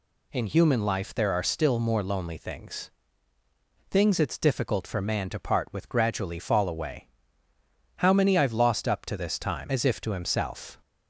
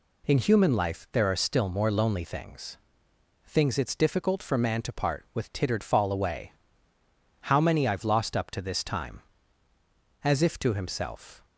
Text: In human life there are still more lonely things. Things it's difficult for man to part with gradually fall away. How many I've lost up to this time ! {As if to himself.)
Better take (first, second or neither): first